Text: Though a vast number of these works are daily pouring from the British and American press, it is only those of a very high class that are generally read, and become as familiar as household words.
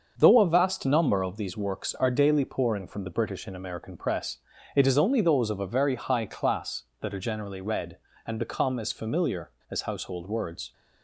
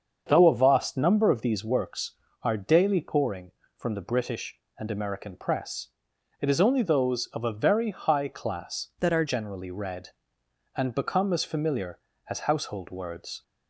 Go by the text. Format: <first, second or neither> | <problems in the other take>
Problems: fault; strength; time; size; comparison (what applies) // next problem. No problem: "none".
first | starts louder than the rest; until 1.2 s; 7 dB; also in the first // changes voice from "that" to "are"; from 8.9 to 9.2 s; 0.3 s long